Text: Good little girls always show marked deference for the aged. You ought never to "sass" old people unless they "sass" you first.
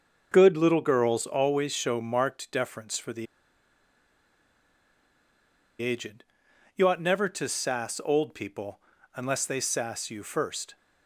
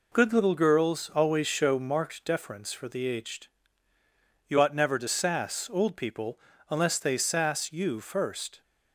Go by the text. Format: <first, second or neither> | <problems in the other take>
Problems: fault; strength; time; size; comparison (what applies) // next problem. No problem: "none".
second | starts louder than the rest; until 1.3 s; 6 dB // pauses between "the" and "aged"; strong; at 3.2 s; 2.5 s long // pauses between "people" and "unless"; at 8.7 s; 0.38 s long; slight in the second